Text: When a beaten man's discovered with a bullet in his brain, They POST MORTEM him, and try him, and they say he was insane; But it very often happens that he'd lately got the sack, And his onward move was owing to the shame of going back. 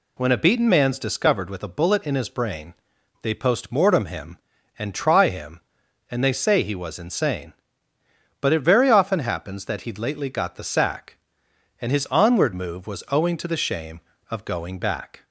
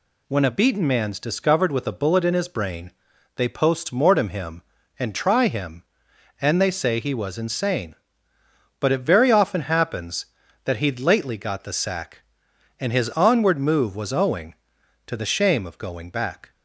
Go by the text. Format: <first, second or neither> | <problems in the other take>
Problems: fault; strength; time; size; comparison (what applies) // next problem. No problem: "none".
neither | none